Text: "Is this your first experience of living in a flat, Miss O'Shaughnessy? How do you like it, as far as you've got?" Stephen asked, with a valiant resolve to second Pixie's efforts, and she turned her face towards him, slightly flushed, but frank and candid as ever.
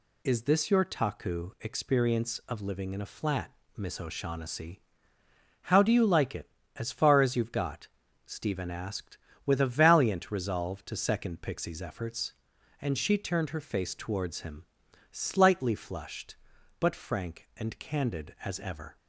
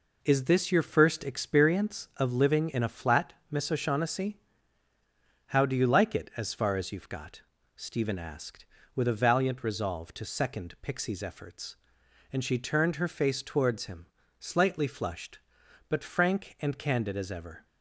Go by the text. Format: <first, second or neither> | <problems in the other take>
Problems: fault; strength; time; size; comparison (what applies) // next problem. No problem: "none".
second | says "taku" for "first"; at 0.8 s